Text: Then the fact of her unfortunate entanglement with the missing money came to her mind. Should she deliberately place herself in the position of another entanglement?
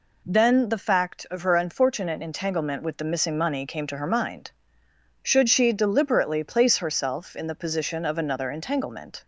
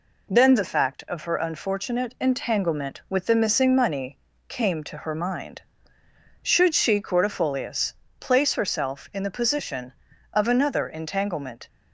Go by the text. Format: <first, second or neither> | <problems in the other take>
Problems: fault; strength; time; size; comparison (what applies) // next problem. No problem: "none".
first | pauses between "money" and "came"; slight; at 4.1 s; 0.28 s long // says "cordifolius" for "deliberately"; at 7.0 s